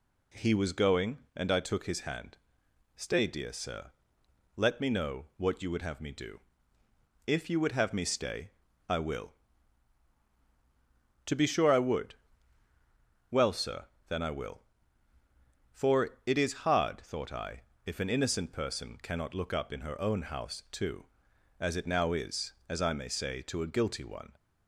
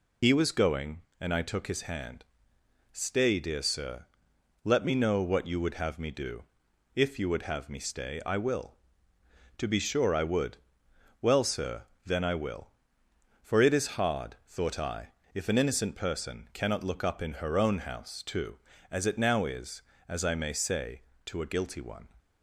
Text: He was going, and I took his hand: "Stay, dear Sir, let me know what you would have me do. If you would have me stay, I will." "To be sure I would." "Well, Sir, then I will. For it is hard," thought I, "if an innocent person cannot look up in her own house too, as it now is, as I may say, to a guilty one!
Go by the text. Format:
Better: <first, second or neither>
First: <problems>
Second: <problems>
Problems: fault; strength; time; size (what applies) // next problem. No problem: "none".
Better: first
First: none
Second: loses the start of "He"; at 0.2 s; 50 ms